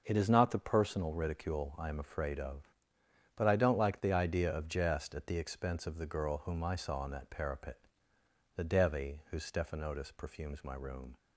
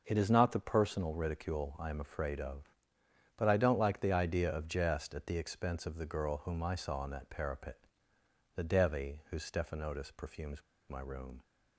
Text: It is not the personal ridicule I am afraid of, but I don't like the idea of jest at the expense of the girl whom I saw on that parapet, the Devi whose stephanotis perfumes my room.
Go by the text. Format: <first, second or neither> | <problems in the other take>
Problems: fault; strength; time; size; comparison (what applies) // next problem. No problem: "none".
first | pauses between "perfumes" and "my"; slight; at 10.6 s; 0.27 s long